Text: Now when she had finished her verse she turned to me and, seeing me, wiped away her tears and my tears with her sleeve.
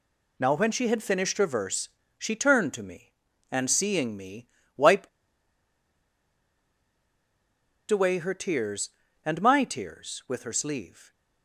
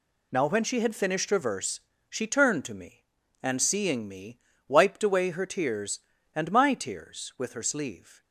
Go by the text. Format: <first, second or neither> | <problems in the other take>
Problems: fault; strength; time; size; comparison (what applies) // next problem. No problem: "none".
second | pauses between "verse" and "she"; slight; at 1.8 s; 0.28 s long; slight in the second // pauses between "wiped" and "away"; strong; at 5.0 s; 2.8 s long